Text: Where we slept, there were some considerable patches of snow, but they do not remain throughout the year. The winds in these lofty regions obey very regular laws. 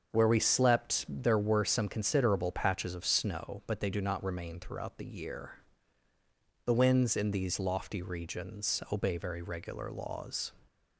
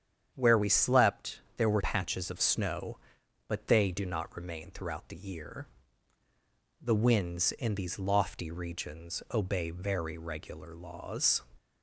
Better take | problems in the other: first | starts louder than the rest; strong; until 1.3 s; 8.5 dB; also in the first // skips "some considerable"; at 1.8 s

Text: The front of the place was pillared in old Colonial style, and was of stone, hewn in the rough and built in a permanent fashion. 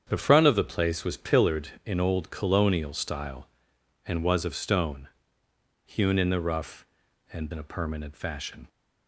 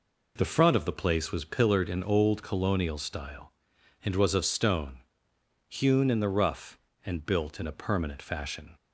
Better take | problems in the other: second | starts louder than the rest; strong; until 1.1 s; 8 dB // skips "built"; at 7.5 s

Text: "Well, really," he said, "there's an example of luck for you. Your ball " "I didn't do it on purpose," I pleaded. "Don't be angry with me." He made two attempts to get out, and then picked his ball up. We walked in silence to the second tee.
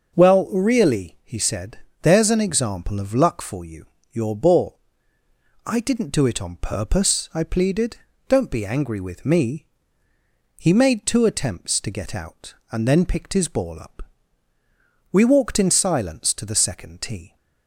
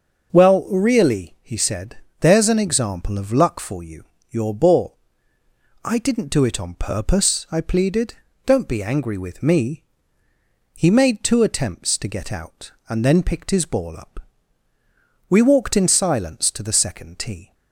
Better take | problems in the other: neither | starts louder than the rest; the same in both

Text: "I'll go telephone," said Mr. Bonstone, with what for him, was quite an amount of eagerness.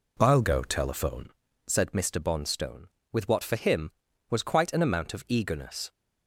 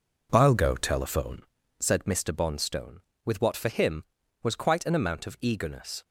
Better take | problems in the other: first | gets quieter; strong; throughout; 8 dB

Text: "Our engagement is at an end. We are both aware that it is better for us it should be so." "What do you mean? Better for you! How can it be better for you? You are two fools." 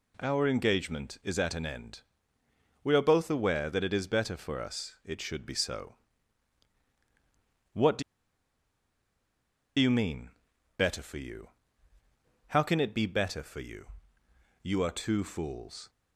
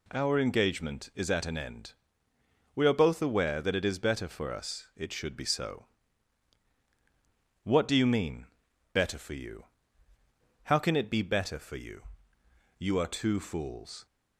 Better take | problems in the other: second | pauses between "do" and "you"; strong; at 8.0 s; 1.7 s long

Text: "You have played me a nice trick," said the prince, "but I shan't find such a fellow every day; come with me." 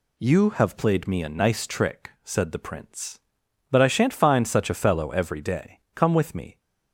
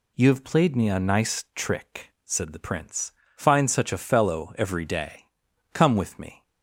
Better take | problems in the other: first | skips "but I shan't"; at 3.2 s

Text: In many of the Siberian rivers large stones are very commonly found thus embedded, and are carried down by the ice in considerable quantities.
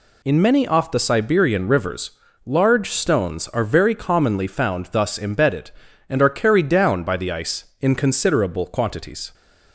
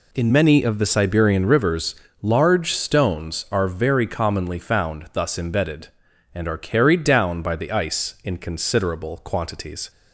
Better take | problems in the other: second | says "off" for "of"; at 0.6 s // pauses between "rivers" and "large"; slight; at 2.1 s; 0.34 s long; slight in the second

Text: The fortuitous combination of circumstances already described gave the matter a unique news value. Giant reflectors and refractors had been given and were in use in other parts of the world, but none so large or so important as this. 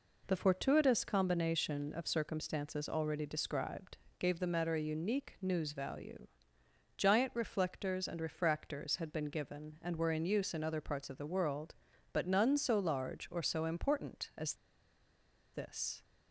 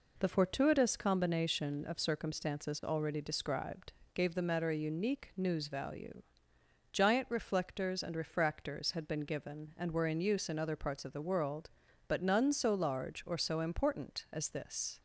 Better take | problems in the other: second | pauses between "described" and "gave"; slight; at 3.9 s; 0.20 s long; slight in the second // pauses between "as" and "this"; at 14.5 s; 0.99 s long

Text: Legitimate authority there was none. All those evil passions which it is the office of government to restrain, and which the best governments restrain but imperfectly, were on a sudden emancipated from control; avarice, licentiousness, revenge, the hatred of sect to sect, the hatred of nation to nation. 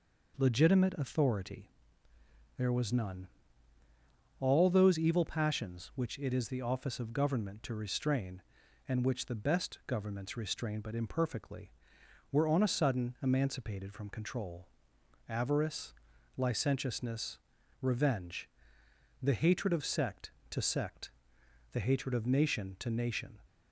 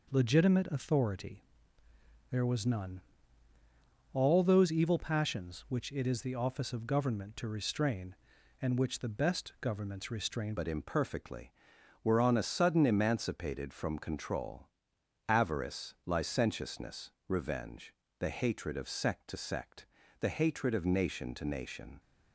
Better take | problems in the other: first | pauses between "authority" and "there"; noticeable; at 1.4 s; 0.88 s long; noticeable in the first // changes voice at "but"; from 10.5 s on; 11.4 s long

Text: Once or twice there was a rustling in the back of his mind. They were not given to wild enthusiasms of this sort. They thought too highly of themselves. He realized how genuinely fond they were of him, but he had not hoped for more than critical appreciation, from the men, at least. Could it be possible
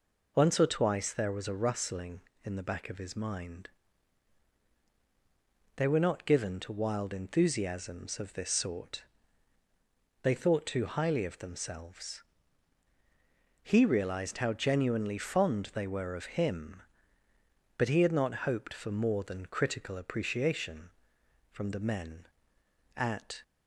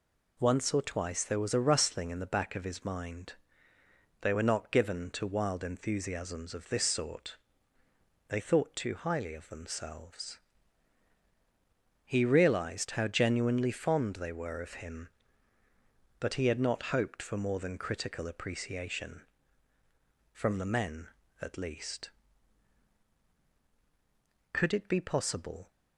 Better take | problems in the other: second | stops before "least Could it be possible"; at 23.4 s

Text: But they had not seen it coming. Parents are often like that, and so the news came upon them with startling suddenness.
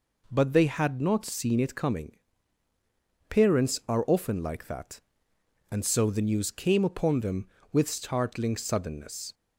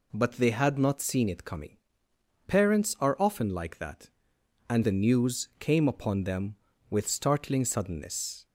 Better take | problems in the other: first | skips "so"; at 4.8 s

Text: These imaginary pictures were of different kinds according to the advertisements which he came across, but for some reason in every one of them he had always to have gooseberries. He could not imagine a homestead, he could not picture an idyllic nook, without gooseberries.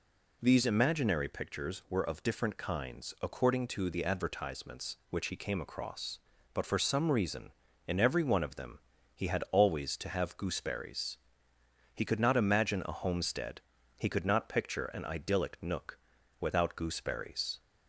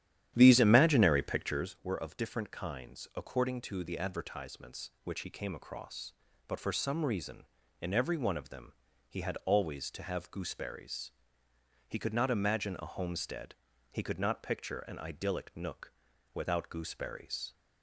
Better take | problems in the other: first | starts louder than the rest; strong; until 1.7 s; 11 dB // pauses between "them" and "he"; slight; at 8.7 s; 0.36 s long; slight in the first

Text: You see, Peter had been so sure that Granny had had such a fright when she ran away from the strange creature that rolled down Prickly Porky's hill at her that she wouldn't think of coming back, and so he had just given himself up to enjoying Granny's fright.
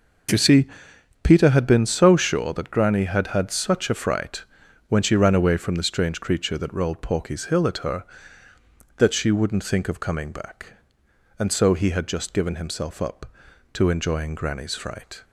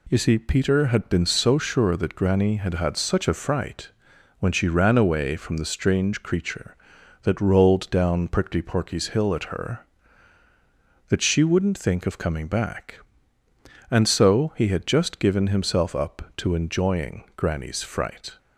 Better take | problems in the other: second | pauses between "fright" and "when"; at 4.4 s; 0.44 s long; noticeable in the second // skips "down Prickly"; at 7.0 s

